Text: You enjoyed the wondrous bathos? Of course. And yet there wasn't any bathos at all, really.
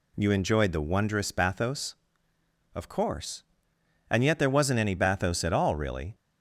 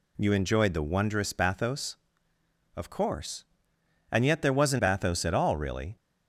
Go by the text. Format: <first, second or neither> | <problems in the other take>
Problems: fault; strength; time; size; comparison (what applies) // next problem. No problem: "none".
first | skips "any"; at 4.7 s